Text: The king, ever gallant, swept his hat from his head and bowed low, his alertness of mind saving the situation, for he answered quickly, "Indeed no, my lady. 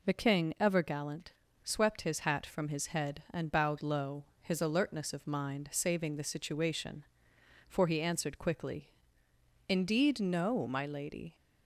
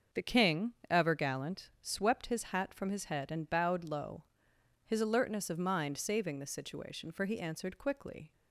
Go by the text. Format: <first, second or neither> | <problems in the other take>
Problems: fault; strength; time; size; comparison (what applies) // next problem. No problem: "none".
first | starts louder than the rest; until 1.3 s; 6.5 dB // stops before "Indeed no my lady"; at 8.3 s